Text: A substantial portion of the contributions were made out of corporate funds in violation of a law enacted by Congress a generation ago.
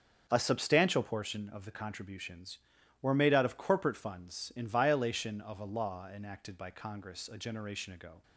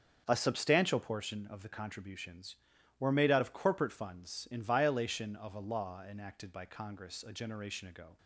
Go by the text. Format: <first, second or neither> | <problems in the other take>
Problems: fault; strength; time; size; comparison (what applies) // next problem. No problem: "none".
neither | starts louder than the rest; strong; the same in both